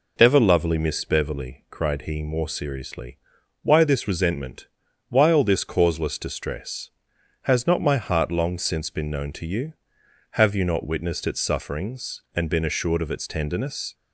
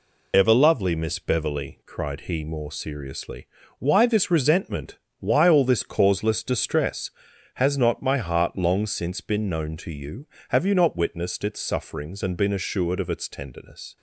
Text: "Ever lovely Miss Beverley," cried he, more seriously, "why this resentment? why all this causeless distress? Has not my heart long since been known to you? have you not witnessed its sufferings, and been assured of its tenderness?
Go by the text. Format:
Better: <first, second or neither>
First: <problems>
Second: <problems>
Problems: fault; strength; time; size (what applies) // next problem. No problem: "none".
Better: first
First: none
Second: loses the start of "Ever"; at 0.3 s; 40 ms